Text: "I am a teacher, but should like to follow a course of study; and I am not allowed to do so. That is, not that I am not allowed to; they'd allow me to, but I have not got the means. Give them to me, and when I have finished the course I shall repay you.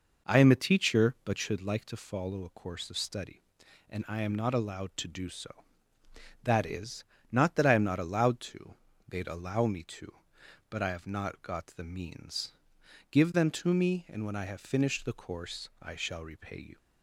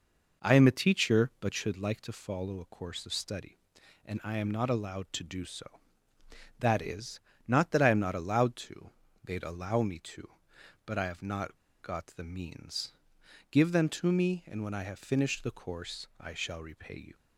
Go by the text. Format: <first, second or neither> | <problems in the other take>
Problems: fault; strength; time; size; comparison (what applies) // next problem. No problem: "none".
first | pauses between "not" and "got"; slight; at 11.5 s; 0.25 s long